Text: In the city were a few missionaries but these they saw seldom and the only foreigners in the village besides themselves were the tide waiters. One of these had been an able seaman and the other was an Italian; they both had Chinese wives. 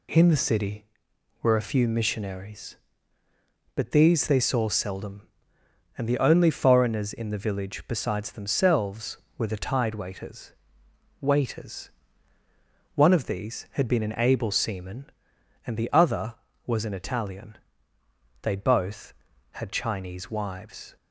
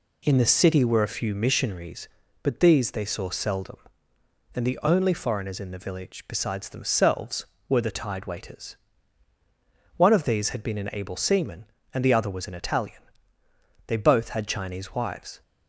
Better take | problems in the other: second | says "waiters" twice; at 11.1 s

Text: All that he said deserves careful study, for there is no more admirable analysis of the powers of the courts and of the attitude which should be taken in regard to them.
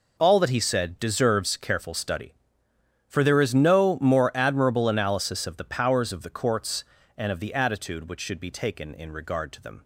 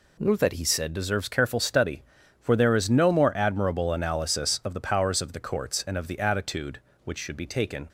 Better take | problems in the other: first | stops before "in regard to them"; at 7.8 s

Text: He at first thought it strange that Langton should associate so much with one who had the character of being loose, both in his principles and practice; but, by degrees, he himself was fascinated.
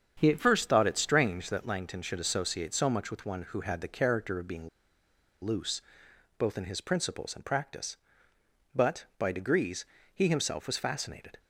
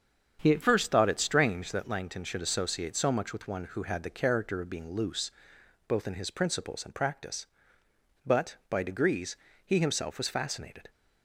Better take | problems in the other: second | starts louder than the rest; strong; until 1.1 s; 7.5 dB; strong in the second // pauses between "being" and "loose"; noticeable; at 4.6 s; 0.75 s long

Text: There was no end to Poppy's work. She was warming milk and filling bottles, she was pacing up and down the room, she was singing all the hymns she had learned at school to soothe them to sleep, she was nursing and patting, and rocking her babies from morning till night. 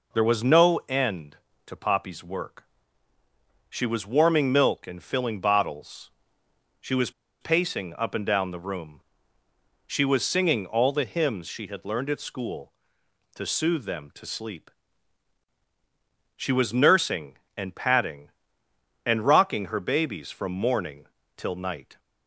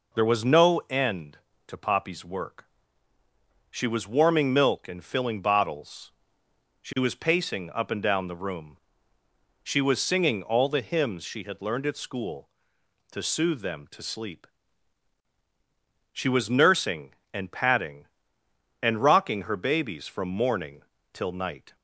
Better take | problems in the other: second | pauses between "was" and "pacing"; slight; at 7.1 s; 0.30 s long // pauses between "morning" and "till"; slight; at 21.0 s; 0.30 s long; slight in the second

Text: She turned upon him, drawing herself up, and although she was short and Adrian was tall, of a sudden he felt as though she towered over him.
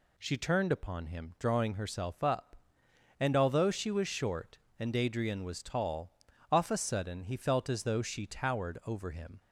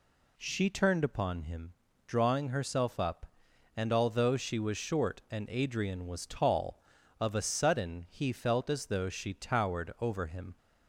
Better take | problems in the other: second | says "off" for "of"; at 6.5 s

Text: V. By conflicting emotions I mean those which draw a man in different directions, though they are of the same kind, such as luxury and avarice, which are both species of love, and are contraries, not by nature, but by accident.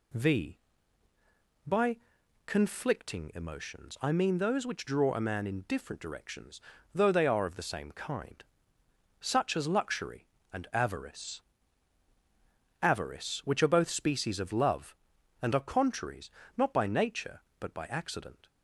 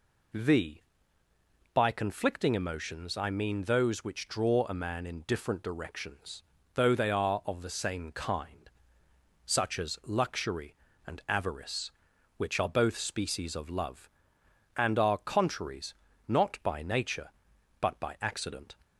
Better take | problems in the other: second | pauses between "By" and "conflicting"; noticeable; at 1.9 s; 0.48 s long // says "avarice" twice; at 12.8 s

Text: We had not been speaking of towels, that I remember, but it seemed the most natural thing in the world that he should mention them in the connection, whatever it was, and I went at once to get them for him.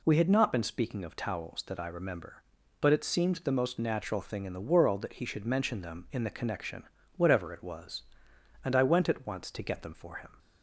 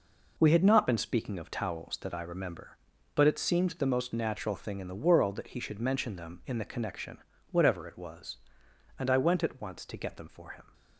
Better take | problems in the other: first | gets quieter; strong; throughout; 9 dB

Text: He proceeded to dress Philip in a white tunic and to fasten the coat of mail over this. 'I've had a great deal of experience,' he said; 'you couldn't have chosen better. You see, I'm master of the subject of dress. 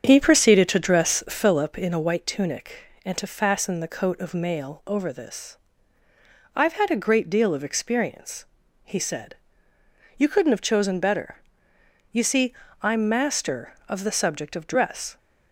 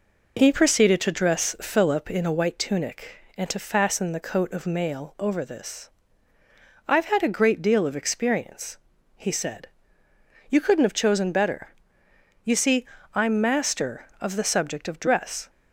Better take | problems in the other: second | starts louder than the rest; strong; until 1.6 s; 7.5 dB

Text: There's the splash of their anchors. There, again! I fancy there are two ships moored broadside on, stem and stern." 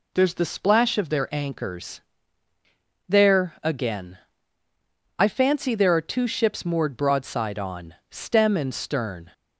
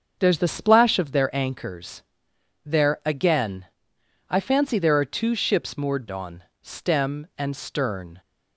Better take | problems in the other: first | starts louder than the rest; until 1.2 s; 6.5 dB // skips "broadside"; at 6.0 s

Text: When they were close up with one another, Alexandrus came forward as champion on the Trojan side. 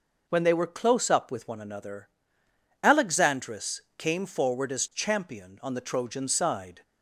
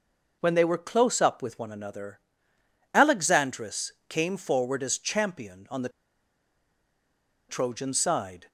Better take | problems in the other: first | pauses between "Alexandrus" and "came"; slight; at 3.9 s; 0.16 s long; slight in the first // pauses between "the" and "Trojan"; strong; at 5.8 s; 1.6 s long

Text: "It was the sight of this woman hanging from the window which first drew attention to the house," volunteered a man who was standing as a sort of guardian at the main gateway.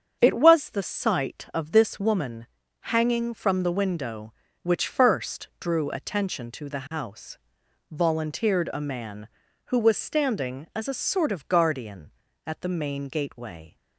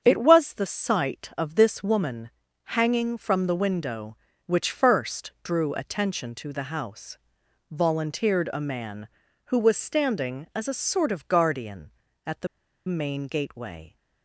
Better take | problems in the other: first | starts louder than the rest; strong; until 1.0 s; 7.5 dB; strong in the first // pauses between "woman" and "hanging"; slight; at 2.3 s; 0.32 s long; slight in the first // pauses between "the" and "main"; at 12.4 s; 0.39 s long

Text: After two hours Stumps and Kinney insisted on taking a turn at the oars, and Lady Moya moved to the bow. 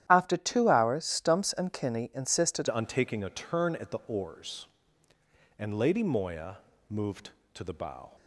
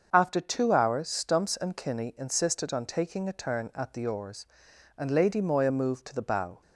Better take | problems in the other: second | starts louder than the rest; strong; until 1.1 s; 11 dB; also in the second // changes voice at "on"; from 2.6 s on; 5.5 s long // pauses between "Moya" and "moved"; slight; at 6.5 s; 0.32 s long

